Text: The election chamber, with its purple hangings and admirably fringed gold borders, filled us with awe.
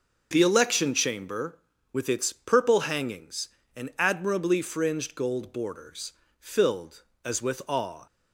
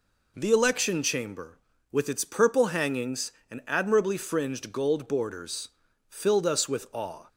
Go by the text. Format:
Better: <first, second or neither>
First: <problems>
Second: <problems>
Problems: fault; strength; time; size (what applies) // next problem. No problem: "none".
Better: second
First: says "as" for "us"; at 7.2 s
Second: none